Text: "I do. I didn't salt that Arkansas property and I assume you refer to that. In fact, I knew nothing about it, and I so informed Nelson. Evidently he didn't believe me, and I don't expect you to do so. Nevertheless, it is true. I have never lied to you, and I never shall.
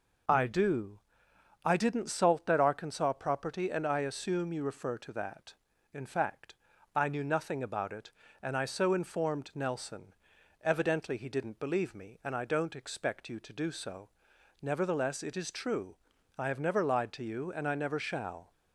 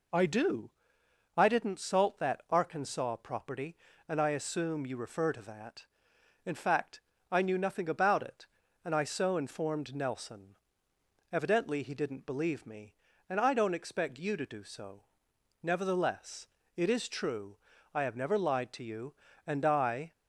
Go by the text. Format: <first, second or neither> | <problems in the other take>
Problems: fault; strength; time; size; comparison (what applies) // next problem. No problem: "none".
first | stops before "never shall"; at 20.1 s